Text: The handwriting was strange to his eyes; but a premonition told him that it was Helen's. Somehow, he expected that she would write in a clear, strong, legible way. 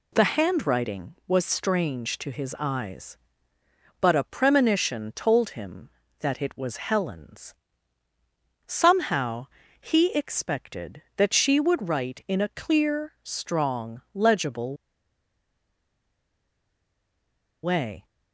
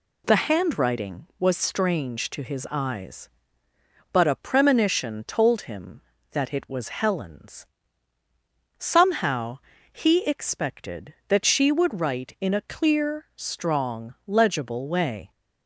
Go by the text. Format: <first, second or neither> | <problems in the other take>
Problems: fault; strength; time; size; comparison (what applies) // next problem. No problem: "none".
second | pauses between "legible" and "way"; strong; at 14.7 s; 2.8 s long